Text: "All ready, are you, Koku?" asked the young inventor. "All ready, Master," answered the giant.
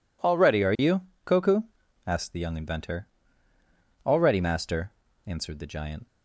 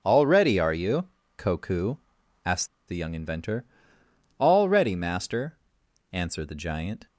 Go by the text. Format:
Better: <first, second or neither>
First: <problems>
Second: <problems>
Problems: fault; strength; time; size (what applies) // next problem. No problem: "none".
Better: first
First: none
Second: pauses between "asked" and "the"; slight; at 2.6 s; 0.20 s long